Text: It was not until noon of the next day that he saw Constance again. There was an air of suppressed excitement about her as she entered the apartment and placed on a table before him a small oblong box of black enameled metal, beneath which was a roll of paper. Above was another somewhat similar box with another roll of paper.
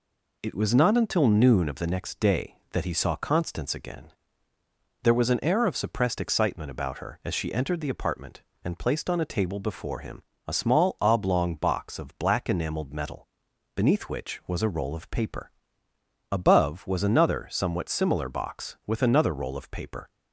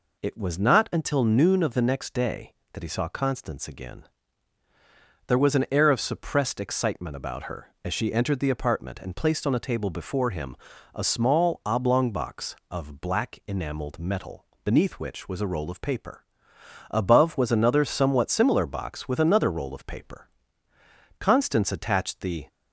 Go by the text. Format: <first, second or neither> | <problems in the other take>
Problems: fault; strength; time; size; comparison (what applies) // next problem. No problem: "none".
first | pauses between "him" and "a"; at 10.5 s; 0.38 s long; slight in the first // goes on to say "Constance attached the"; noticeable; from 21.1 s on; 1.2 s long